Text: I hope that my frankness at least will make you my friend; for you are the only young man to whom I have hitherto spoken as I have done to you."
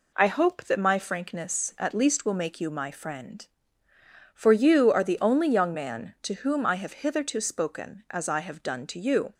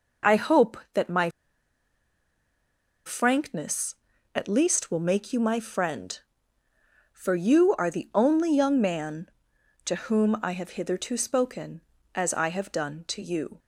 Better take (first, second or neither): first